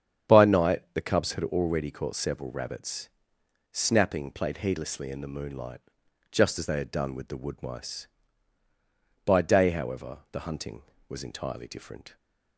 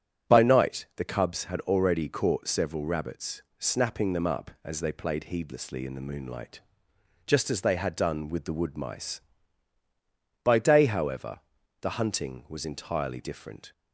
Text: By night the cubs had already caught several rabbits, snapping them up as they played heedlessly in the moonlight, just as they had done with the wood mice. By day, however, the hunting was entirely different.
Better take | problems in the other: second | starts louder than the rest; strong; until 1.4 s; 8.5 dB; strong in the second // skips "them up as they"; at 4.3 s

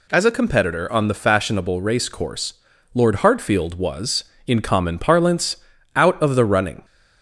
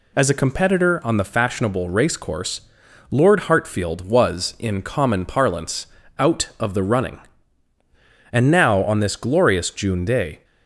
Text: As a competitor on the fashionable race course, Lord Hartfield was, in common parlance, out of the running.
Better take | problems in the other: first | goes on to say "And now on this glorious June day"; strong; from 8.3 s on; 2.1 s long

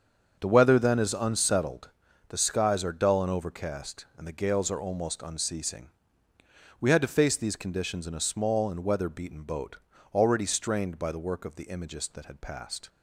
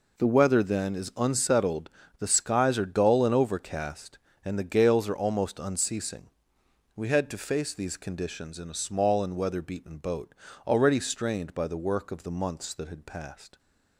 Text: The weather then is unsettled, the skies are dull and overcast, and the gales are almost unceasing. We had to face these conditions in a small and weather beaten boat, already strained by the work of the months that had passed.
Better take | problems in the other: second | starts louder than the rest; until 1.4 s; 7 dB // says "imagist" for "months"; at 11.6 s

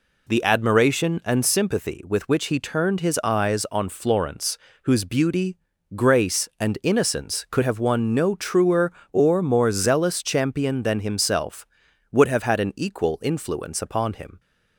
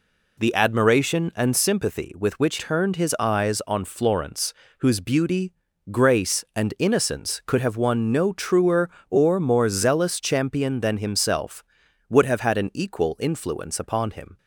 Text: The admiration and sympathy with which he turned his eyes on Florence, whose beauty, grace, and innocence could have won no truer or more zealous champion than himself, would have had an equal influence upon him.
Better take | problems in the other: first | skips "he"; at 2.5 s

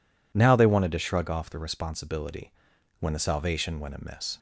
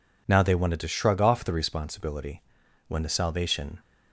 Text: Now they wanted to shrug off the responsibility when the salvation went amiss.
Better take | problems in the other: first | pauses between "responsibility" and "when"; noticeable; at 2.4 s; 0.46 s long; noticeable in the first // stops before "went amiss"; at 3.7 s

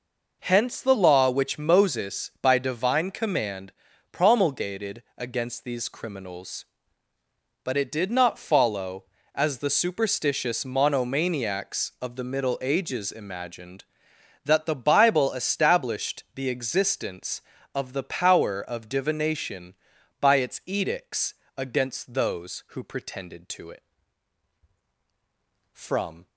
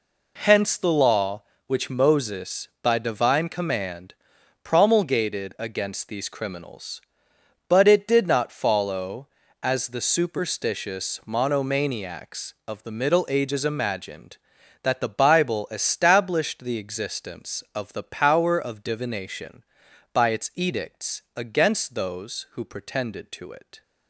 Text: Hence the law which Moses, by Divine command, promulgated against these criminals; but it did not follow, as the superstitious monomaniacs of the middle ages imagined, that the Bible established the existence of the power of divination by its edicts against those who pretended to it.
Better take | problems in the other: second | pauses between "edicts" and "against"; slight; at 21.3 s; 0.24 s long // goes on to say "From"; from 25.7 s on; 0.54 s long

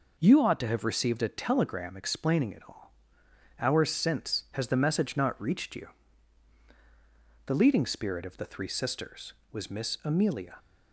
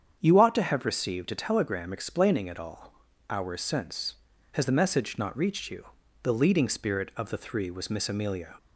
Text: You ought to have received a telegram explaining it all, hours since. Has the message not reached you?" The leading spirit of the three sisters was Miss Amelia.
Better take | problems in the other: first | starts louder than the rest; strong; until 1.2 s; 8 dB // skips "sisters"; at 7.6 s

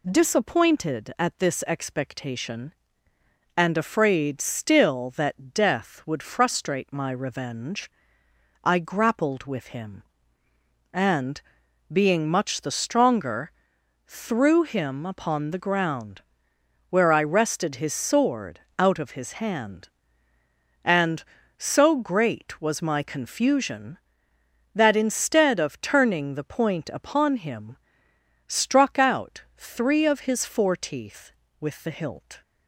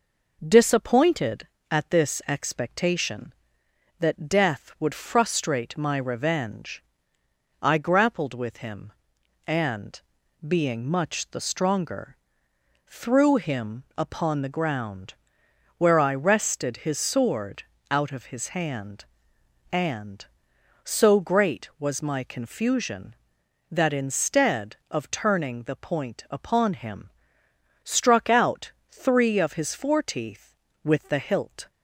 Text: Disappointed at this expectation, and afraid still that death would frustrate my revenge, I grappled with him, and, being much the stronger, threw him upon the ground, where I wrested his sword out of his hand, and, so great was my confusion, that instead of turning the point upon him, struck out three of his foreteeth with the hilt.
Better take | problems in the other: first | skips "and afraid still"; at 3.6 s // pauses between "sword" and "out"; slight; at 17.6 s; 0.28 s long; slight in the first // pauses between "out" and "three"; slight; at 28.7 s; 0.20 s long; slight in the first

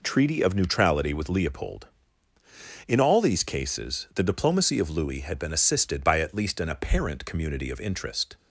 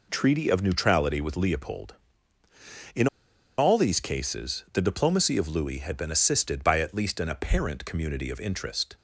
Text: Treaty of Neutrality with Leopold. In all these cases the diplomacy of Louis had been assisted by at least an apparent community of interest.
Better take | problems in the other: first | pauses between "In" and "all"; noticeable; at 3.0 s; 0.51 s long

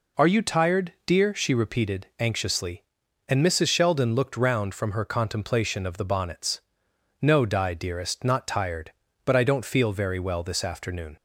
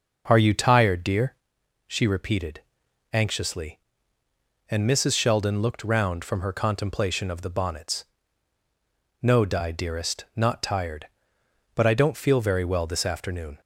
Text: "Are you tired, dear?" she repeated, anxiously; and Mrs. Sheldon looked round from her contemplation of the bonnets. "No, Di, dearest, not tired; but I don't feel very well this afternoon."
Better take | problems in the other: first | starts louder than the rest; noticeable; until 1.6 s; 6 dB

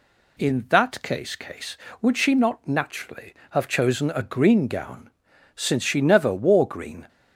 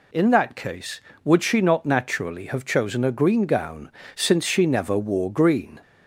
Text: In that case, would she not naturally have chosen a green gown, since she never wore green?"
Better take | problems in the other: second | says "case" twice; at 1.3 s

